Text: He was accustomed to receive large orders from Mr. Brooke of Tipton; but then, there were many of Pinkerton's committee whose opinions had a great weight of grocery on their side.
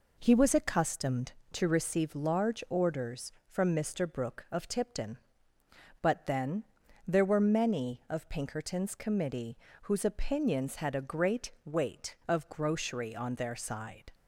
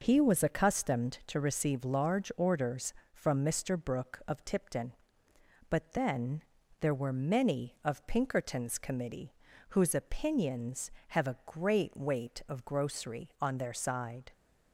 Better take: first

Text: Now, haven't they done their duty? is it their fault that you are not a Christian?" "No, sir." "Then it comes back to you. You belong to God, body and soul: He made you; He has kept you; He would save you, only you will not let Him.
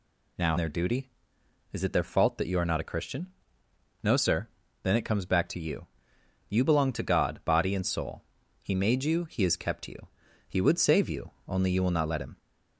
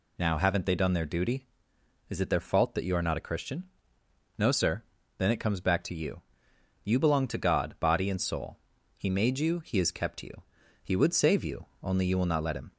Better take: second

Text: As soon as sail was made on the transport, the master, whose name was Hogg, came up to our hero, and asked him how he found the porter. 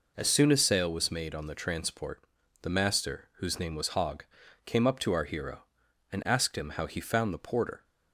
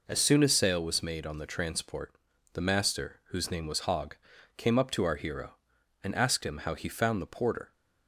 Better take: neither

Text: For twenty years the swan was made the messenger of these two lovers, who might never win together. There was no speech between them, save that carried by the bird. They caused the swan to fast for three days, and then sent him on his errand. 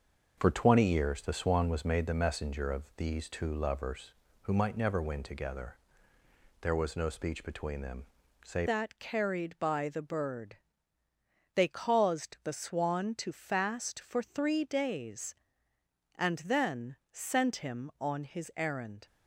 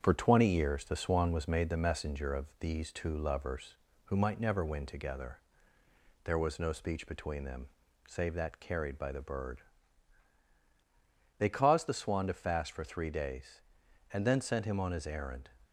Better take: second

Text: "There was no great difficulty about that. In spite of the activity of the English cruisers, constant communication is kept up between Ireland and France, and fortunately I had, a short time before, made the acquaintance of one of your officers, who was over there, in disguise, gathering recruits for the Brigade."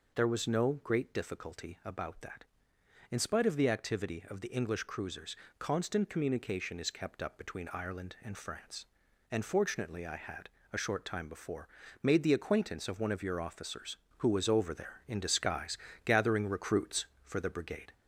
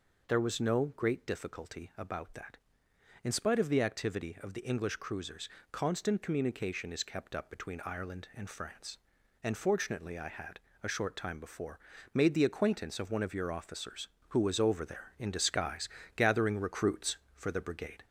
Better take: neither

